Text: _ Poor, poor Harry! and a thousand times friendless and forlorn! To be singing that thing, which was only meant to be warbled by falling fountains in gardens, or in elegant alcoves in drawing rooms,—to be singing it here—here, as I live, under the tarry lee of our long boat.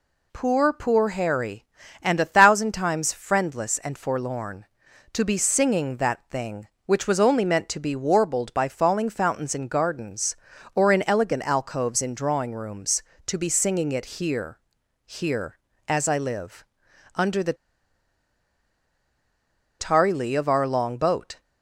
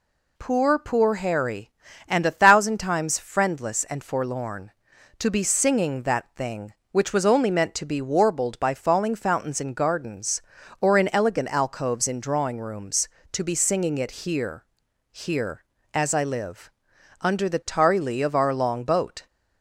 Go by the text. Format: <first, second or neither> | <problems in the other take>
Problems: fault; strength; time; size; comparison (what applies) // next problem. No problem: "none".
second | pauses between "the" and "tarry"; strong; at 17.5 s; 2.2 s long